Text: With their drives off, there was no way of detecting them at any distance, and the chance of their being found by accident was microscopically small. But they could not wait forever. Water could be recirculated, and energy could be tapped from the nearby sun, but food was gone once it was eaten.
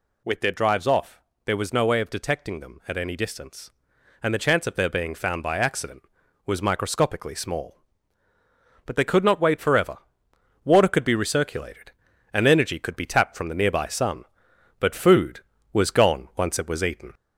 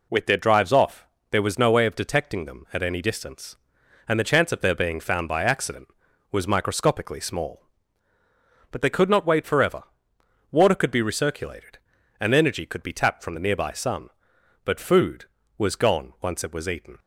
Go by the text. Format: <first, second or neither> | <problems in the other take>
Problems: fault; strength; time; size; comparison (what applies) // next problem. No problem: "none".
second | gets louder; slight; throughout; 2.5 dB